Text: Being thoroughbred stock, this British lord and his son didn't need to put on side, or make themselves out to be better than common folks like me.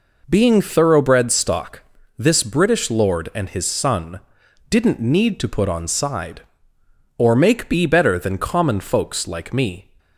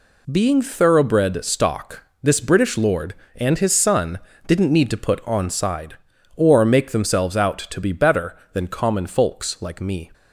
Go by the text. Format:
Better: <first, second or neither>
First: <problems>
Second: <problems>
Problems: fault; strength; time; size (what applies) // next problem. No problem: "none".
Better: second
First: pauses between "son" and "didn't"; noticeable; at 4.2 s; 0.50 s long // skips "themselves out to"; at 7.6 s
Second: pauses between "son" and "didn't"; slight; at 4.1 s; 0.28 s long